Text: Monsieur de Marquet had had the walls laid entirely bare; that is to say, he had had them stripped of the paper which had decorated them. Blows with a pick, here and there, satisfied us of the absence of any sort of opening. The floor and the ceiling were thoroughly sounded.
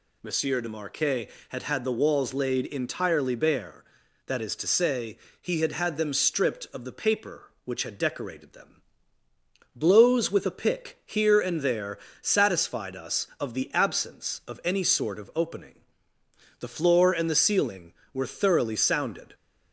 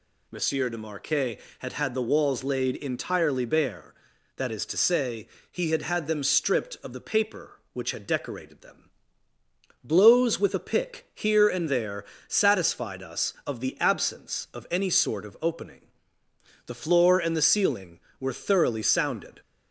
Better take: neither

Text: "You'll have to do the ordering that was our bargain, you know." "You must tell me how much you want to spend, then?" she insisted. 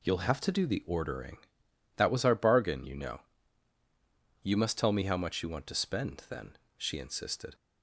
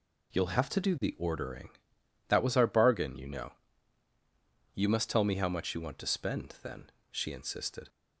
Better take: neither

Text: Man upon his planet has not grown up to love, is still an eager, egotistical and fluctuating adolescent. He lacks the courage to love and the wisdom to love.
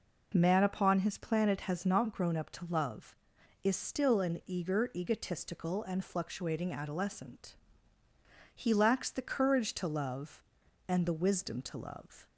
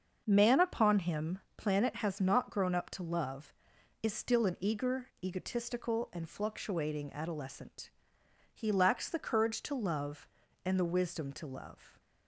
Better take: first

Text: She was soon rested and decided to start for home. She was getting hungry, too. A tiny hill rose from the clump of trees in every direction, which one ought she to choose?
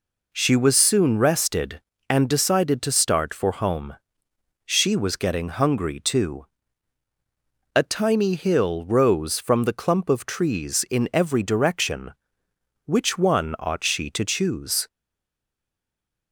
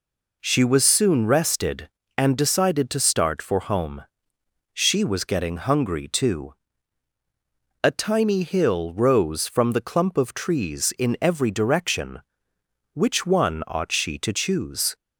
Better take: second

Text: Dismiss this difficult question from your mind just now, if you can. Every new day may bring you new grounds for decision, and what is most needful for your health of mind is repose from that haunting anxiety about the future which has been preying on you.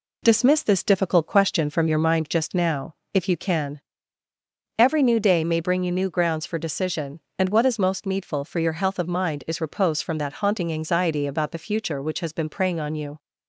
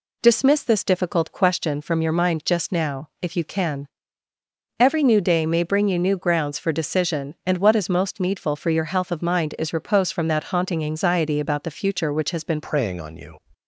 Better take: first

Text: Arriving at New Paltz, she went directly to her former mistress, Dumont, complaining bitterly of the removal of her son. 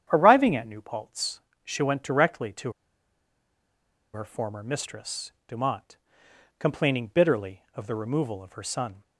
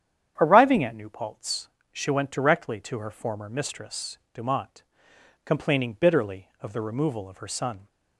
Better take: second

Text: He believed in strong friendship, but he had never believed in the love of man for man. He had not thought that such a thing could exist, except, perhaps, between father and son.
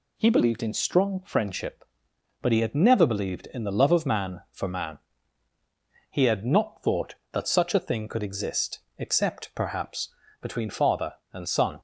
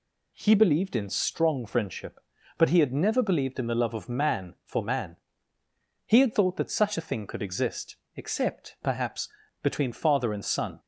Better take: first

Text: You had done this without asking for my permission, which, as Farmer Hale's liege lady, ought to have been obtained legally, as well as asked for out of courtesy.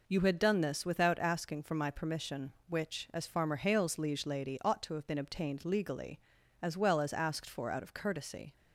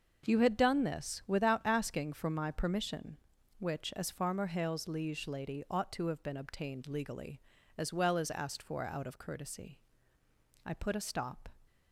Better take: first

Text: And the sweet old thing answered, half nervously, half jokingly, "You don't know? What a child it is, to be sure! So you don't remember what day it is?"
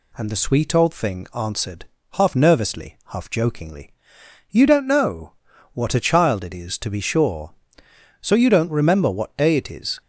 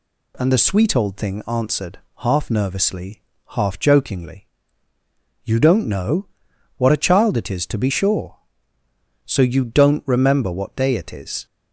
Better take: neither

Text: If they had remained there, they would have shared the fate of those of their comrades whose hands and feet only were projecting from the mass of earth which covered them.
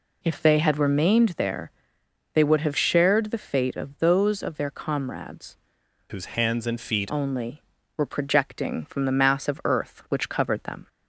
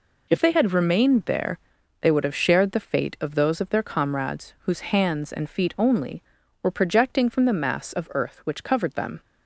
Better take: second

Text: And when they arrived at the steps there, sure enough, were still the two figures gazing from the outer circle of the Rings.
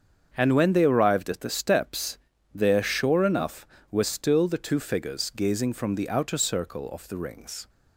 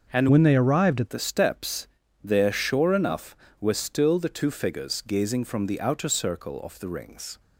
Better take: first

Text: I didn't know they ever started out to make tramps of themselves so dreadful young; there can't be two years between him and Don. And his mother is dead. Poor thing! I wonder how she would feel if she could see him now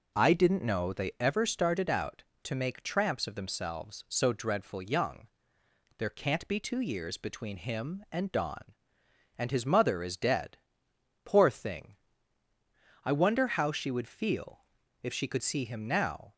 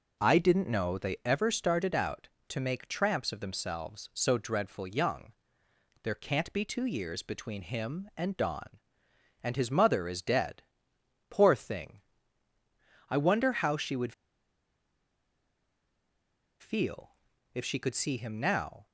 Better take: first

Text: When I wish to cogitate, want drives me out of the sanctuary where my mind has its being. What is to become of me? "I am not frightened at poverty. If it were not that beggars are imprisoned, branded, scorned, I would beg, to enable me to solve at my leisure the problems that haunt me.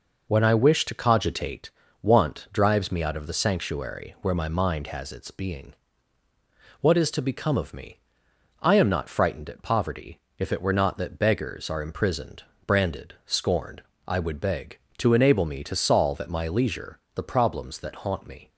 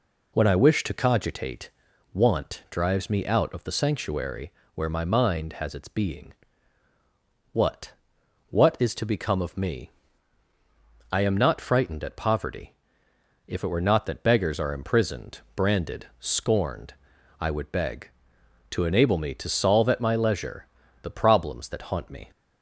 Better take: first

